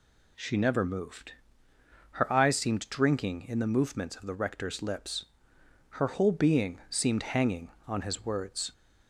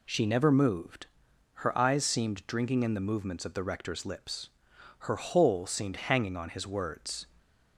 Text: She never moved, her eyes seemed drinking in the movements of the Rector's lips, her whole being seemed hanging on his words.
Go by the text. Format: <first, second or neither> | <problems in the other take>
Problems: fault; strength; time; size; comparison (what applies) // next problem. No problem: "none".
first | skips "being"; at 5.6 s